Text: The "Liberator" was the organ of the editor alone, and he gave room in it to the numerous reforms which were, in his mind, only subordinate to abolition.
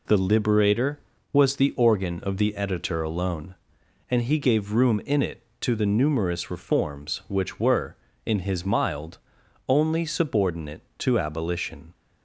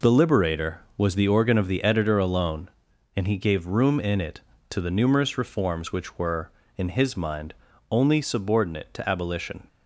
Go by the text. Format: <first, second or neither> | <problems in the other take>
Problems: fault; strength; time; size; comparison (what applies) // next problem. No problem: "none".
second | says "mild" for "mind"; at 8.6 s